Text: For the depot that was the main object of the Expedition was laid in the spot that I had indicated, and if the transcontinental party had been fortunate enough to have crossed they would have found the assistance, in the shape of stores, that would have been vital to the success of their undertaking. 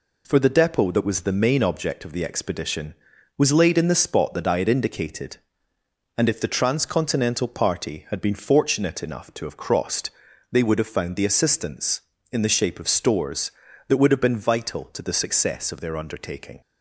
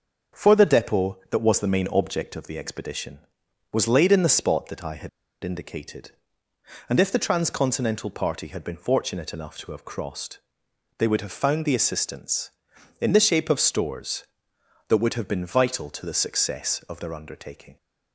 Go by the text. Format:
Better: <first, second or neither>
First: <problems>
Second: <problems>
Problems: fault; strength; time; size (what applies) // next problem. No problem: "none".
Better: first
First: pauses between "crossed" and "they"; at 10.0 s; 0.42 s long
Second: starts louder than the rest; until 1.4 s; 6 dB // pauses between "had" and "indicated"; slight; at 5.0 s; 0.34 s long // pauses between "crossed" and "they"; noticeable; at 10.3 s; 0.60 s long